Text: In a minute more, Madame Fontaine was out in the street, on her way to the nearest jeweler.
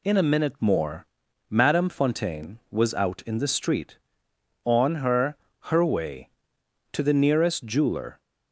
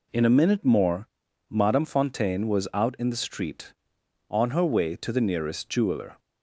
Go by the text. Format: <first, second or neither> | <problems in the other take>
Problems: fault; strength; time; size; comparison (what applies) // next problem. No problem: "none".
second | says "her" twice; at 5.7 s